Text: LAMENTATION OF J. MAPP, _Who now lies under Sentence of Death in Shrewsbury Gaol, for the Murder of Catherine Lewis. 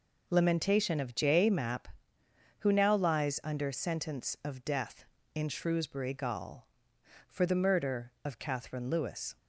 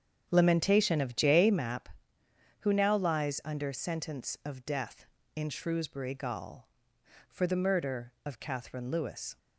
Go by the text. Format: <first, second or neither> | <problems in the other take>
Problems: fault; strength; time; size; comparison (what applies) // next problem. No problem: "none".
first | starts louder than the rest; strong; until 1.7 s; 8 dB